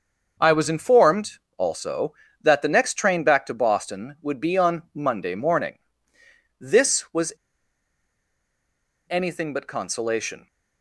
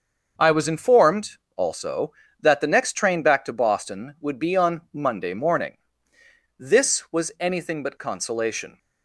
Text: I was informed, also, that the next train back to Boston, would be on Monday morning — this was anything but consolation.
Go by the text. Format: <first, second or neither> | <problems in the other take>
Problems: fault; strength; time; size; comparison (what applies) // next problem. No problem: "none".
second | starts louder than the rest; until 1.6 s; 6.5 dB; also in the second // pauses between "was" and "anything"; strong; at 7.3 s; 1.7 s long